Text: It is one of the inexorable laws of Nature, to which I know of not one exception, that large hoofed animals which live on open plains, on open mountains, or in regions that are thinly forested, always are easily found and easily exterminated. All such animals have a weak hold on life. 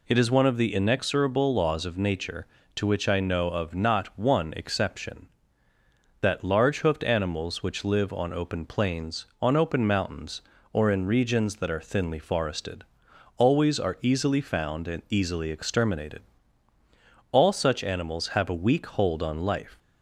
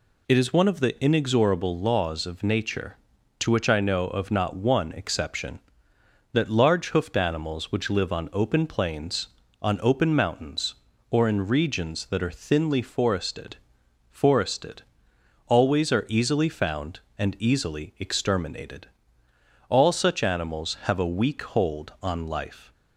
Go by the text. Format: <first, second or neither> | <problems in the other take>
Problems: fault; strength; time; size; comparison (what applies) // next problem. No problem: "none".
first | says "forested" twice; at 14.0 s